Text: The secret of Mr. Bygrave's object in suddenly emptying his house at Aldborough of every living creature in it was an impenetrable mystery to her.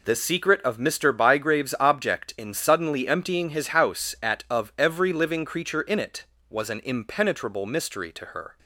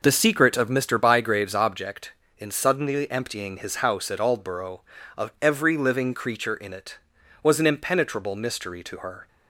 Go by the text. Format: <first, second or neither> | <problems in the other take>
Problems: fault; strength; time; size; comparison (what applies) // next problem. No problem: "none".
second | skips "Aldborough"; at 4.4 s